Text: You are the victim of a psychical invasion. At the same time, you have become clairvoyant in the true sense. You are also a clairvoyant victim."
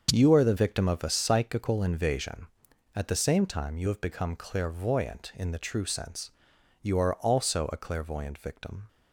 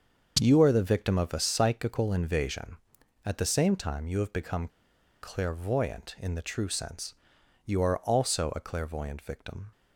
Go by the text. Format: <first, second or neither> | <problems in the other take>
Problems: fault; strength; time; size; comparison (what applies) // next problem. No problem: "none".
first | starts louder than the rest; until 1.4 s; 6.5 dB; also in the first // pauses between "become" and "clairvoyant"; noticeable; at 4.6 s; 0.54 s long